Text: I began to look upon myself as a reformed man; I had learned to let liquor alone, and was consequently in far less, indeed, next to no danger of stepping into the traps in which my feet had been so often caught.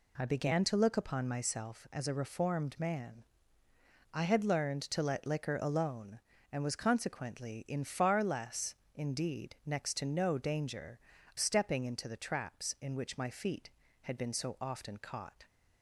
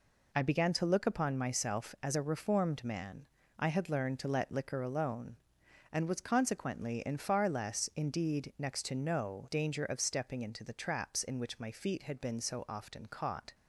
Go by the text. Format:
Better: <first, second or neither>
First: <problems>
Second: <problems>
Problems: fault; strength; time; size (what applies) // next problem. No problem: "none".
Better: second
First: skips "of"; at 11.1 s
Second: none